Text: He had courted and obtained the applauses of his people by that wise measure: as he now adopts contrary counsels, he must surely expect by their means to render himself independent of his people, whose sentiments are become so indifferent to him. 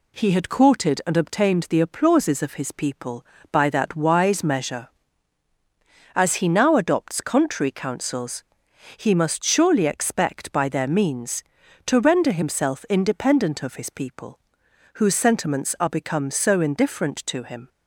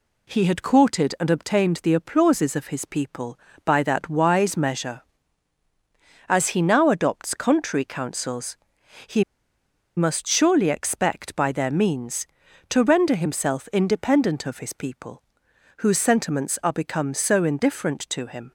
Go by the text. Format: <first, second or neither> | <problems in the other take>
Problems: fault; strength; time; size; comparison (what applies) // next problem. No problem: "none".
first | pauses between "he" and "must"; noticeable; at 9.2 s; 0.74 s long